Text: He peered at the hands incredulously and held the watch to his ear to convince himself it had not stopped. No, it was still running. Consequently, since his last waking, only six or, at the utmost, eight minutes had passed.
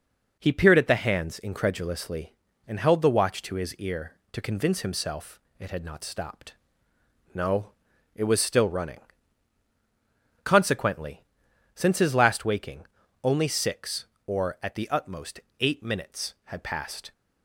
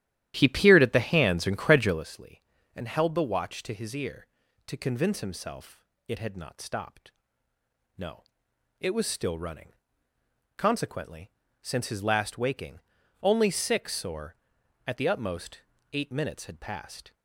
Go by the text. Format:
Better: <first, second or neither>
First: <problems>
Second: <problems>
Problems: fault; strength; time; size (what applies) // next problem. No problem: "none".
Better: first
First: pauses between "himself" and "it"; slight; at 5.3 s; 0.18 s long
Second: starts louder than the rest; strong; until 2.1 s; 12.5 dB // pauses between "himself" and "it"; slight; at 5.8 s; 0.24 s long